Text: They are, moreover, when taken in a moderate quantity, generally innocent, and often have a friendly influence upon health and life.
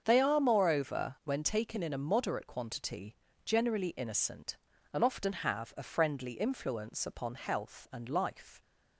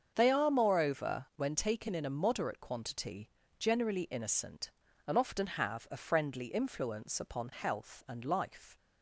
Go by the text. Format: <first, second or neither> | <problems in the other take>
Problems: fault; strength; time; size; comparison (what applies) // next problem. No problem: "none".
neither | starts louder than the rest; the same in both